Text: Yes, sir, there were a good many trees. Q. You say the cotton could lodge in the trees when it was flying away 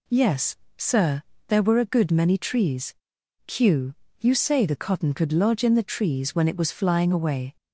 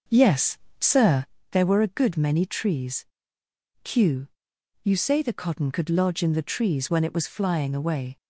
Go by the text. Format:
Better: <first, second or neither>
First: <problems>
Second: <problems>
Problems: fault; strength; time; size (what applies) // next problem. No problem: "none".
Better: first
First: none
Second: starts louder than the rest; until 1.3 s; 6 dB